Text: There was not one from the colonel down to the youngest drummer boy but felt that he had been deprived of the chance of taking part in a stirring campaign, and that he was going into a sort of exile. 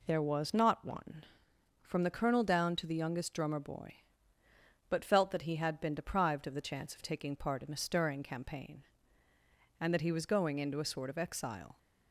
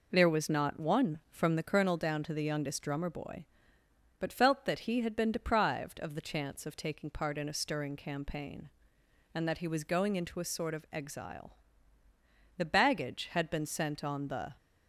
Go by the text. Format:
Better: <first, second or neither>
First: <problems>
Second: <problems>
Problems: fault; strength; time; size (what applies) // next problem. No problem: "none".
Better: first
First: none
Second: goes on to say "The baggage had been sent on the"; strong; from 12.5 s on; 1.9 s long